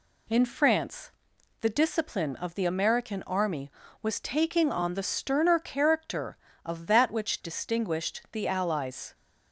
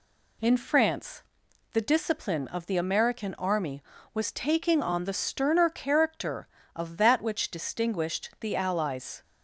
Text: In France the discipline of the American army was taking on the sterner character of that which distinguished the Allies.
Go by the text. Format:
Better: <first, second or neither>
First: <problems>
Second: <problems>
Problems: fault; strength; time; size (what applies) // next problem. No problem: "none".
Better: neither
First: pauses between "France" and "the"; noticeable; at 1.1 s; 0.52 s long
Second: pauses between "France" and "the"; noticeable; at 1.2 s; 0.52 s long